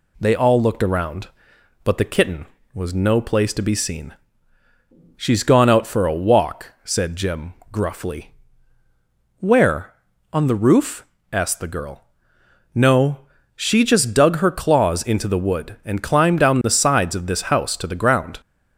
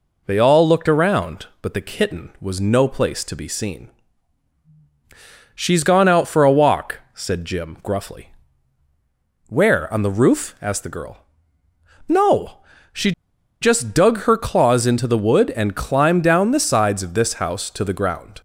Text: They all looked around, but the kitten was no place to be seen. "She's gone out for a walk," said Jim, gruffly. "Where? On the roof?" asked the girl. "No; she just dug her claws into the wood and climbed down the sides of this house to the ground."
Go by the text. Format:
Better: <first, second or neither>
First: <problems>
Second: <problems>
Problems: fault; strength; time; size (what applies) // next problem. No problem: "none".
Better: first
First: none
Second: pauses between "she" and "just"; noticeable; at 13.1 s; 0.50 s long